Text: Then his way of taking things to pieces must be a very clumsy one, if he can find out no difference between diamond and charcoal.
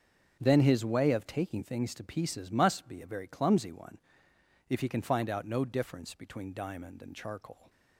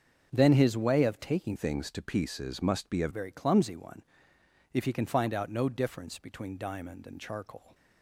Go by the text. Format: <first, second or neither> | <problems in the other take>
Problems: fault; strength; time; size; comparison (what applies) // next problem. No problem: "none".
first | starts louder than the rest; until 1.3 s; 7 dB; also in the first // changes voice from "things" to "a"; from 1.5 to 3.0 s; 1.5 s long